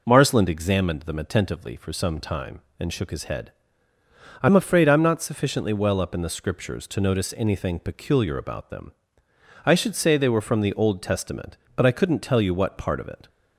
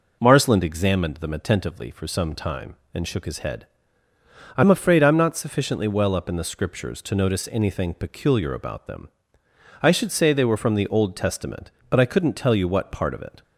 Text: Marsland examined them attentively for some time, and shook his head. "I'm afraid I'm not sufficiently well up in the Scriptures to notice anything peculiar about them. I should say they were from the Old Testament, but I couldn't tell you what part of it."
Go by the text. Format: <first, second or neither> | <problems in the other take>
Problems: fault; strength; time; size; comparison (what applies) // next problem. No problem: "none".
neither | none